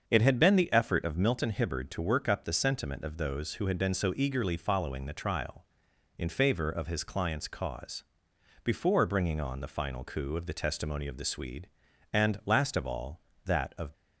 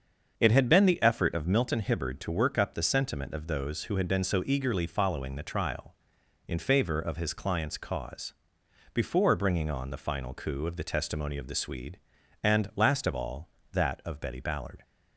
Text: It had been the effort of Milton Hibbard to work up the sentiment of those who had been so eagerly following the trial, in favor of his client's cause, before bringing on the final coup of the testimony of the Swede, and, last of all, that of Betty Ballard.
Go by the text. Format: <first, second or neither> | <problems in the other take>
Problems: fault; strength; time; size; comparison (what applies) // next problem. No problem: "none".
second | starts louder than the rest; until 1.0 s; 7 dB; also in the second // stops before "Betty Ballard"; at 13.9 s